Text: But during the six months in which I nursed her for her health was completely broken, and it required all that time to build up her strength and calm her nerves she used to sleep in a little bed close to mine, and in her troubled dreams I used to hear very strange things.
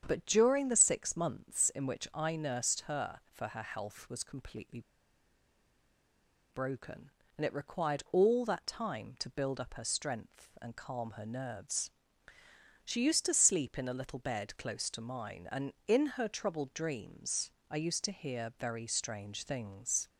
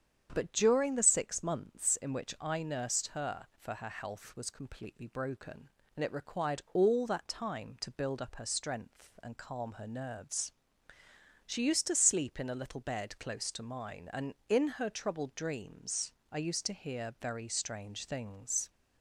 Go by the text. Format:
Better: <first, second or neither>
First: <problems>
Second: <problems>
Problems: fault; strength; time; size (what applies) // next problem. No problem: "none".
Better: second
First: starts louder than the rest; strong; until 1.0 s; 8 dB // pauses between "completely" and "broken"; strong; at 4.8 s; 1.7 s long // pauses between "nerves" and "she"; noticeable; at 11.9 s; 0.94 s long // pauses between "dreams" and "I"; slight; at 17.5 s; 0.18 s long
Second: starts louder than the rest; strong; until 1.3 s; 8 dB // pauses between "nerves" and "she"; noticeable; at 10.5 s; 0.94 s long // pauses between "dreams" and "I"; slight; at 16.1 s; 0.18 s long